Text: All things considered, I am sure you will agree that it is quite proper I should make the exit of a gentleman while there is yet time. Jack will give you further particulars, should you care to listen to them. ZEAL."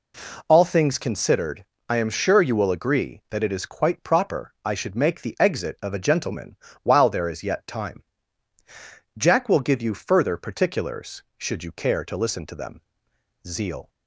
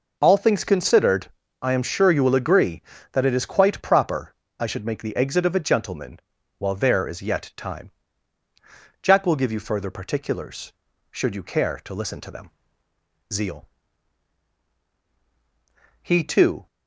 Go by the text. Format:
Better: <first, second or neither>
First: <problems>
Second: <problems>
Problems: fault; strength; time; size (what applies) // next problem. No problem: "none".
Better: first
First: pauses between "gentleman" and "while"; slight; at 6.5 s; 0.28 s long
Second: pauses between "proper" and "I"; slight; at 4.3 s; 0.28 s long // pauses between "gentleman" and "while"; at 6.2 s; 0.38 s long // goes on to say "He too"; noticeable; from 16.0 s on; 0.66 s long